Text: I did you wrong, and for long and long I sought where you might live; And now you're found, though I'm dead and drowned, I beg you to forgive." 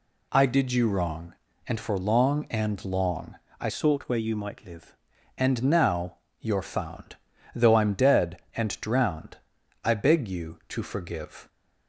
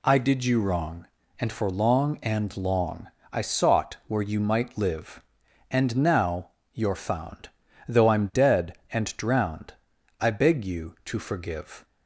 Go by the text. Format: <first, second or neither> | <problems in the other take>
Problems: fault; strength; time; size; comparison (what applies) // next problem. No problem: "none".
second | pauses between "long" and "I"; slight; at 3.3 s; 0.26 s long; slight in the second // changes voice from "sought" to "live"; from 3.6 to 4.9 s; 1.3 s long // pauses between "now" and "you're"; slight; at 6.1 s; 0.22 s long; slight in the second